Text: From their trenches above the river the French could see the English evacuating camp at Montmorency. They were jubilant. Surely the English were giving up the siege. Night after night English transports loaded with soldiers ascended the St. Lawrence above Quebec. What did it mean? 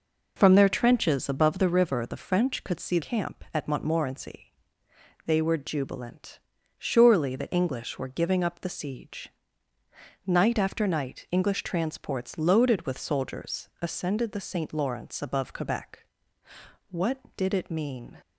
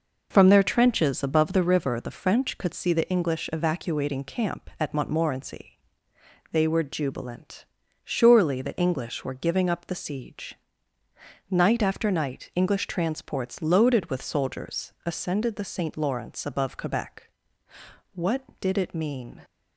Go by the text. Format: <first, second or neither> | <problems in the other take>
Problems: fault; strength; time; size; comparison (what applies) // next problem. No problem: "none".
second | skips "the English evacuating"; at 2.9 s